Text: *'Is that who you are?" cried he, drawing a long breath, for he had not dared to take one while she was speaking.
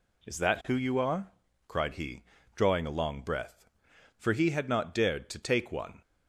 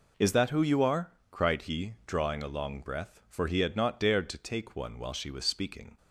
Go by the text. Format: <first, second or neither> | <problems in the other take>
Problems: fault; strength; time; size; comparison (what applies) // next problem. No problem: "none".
second | stops before "while she was speaking"; at 6.0 s